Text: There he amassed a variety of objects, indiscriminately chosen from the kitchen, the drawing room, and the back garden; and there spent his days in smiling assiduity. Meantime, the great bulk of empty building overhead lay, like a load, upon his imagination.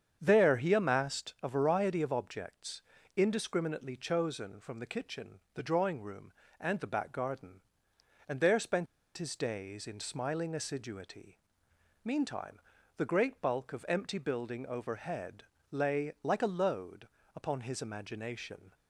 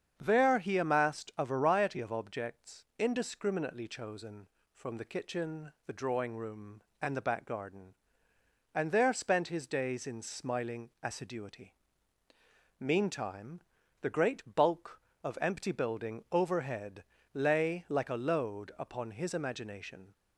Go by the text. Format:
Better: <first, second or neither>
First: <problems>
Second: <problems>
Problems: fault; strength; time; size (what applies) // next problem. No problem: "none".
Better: second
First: starts louder than the rest; strong; until 1.2 s; 8 dB // pauses between "spent" and "his"; slight; at 8.8 s; 0.31 s long // pauses between "overhead" and "lay"; slight; at 15.4 s; 0.28 s long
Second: starts louder than the rest; strong; until 1.1 s; 7.5 dB // pauses between "overhead" and "lay"; slight; at 17.0 s; 0.28 s long